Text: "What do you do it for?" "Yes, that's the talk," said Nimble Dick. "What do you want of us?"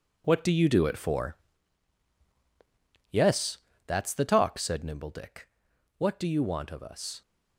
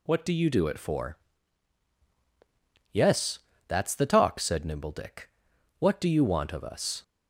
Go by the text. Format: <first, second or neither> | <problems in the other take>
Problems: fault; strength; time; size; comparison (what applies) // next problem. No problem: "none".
second | gets quieter; strong; throughout; 10 dB